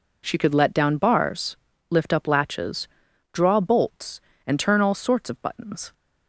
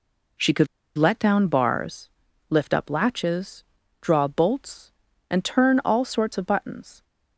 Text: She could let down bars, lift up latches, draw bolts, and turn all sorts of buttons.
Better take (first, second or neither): first